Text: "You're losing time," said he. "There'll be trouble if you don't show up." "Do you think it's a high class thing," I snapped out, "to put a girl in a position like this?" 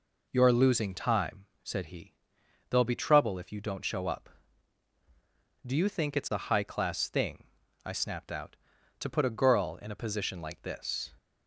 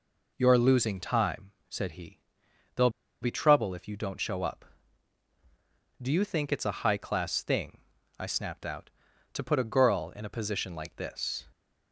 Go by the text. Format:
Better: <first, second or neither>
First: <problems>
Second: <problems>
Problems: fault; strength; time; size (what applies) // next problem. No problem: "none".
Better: first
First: none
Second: pauses between "There'll" and "be"; slight; at 2.8 s; 0.32 s long